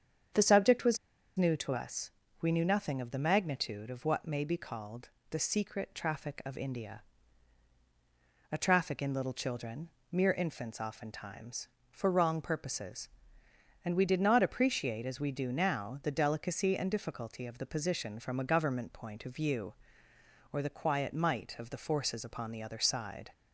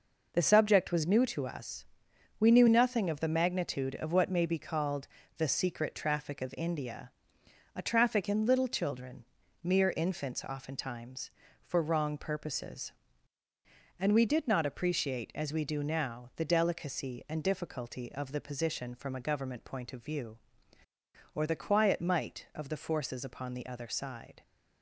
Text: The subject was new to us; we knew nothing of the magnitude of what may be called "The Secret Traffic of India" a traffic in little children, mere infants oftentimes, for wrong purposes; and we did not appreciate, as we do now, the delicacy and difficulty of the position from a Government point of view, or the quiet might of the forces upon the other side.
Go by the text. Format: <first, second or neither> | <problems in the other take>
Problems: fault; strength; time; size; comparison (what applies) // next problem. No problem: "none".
second | starts louder than the rest; strong; until 1.7 s; 7.5 dB // pauses between "was" and "new"; at 0.9 s; 0.40 s long // pauses between "called" and "The"; slight; at 5.0 s; 0.20 s long; slight in the second // pauses between "India" and "a"; strong; at 7.0 s; 1.4 s long; noticeable in the second